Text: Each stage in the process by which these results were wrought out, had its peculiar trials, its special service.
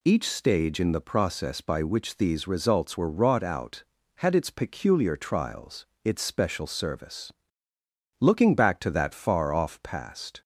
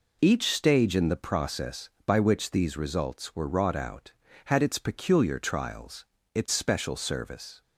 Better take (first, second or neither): second